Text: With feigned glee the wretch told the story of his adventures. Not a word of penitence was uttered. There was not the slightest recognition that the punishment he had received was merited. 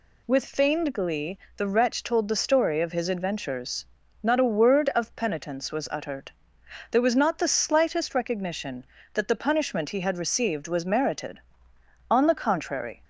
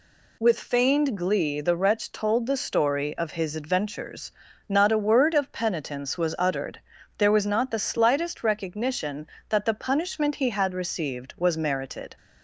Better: second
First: pauses between "glee" and "the"; slight; at 1.3 s; 0.20 s long // goes on to say "On the contrary"; noticeable; from 12.0 s on; 0.94 s long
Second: none

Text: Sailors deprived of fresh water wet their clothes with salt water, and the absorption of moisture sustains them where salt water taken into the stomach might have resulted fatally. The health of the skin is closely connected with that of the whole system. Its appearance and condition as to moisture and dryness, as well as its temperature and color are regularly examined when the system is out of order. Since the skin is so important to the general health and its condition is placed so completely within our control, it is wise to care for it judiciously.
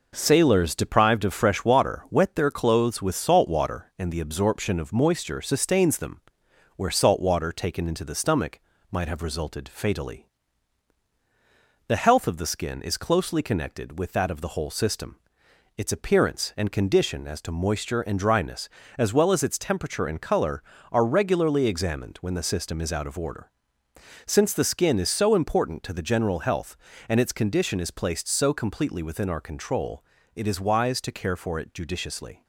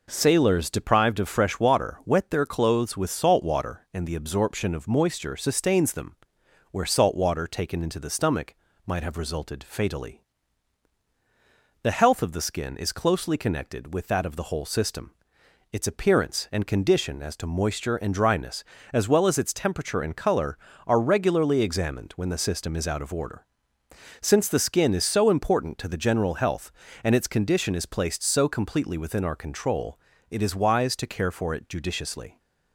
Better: second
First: gets quieter; throughout; 3.5 dB // pauses between "them" and "where"; noticeable; at 6.1 s; 0.56 s long // pauses between "stomach" and "might"; slight; at 8.5 s; 0.32 s long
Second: pauses between "them" and "where"; noticeable; at 6.1 s; 0.56 s long // pauses between "stomach" and "might"; slight; at 8.5 s; 0.32 s long

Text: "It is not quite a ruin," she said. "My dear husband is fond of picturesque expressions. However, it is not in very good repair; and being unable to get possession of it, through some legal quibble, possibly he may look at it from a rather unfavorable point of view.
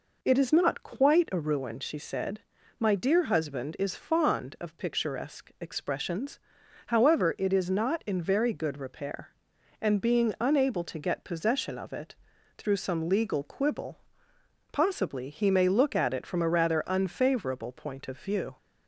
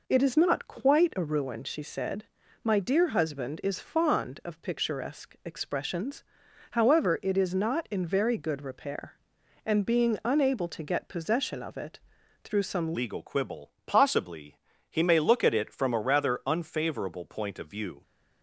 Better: first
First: none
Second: changes voice at "legal"; from 12.9 s on; 5.1 s long // pauses between "possibly" and "he"; slight; at 14.5 s; 0.28 s long

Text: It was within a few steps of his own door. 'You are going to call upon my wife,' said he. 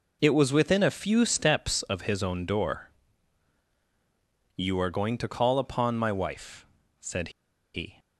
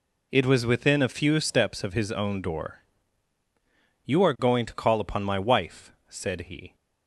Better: second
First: pauses between "said" and "he"; at 7.2 s; 0.44 s long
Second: none

